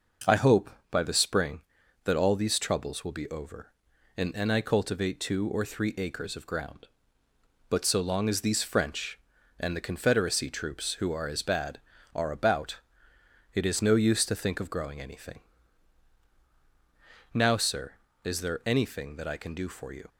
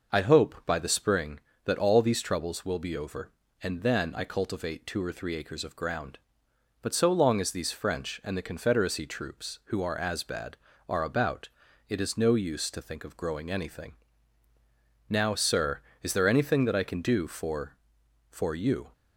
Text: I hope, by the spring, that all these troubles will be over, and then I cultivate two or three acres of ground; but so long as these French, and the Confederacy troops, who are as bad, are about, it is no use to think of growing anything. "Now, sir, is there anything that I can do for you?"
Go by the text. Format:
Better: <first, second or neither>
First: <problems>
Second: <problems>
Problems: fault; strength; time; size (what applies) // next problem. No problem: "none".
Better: first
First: none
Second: says "for" twice; at 18.3 s